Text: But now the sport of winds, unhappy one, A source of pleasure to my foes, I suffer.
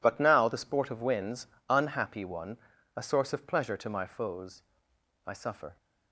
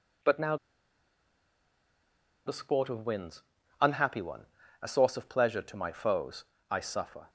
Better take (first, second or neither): first